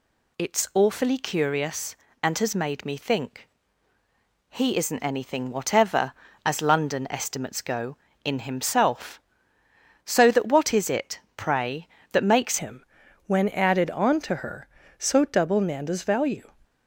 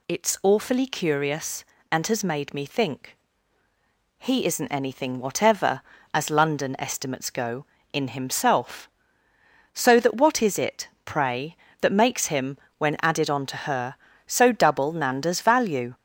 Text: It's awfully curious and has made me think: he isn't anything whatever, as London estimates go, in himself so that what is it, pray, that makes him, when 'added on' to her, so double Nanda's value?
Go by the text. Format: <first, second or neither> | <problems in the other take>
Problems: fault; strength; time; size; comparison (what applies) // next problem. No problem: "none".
second | changes voice at "him"; from 12.5 s on; 3.9 s long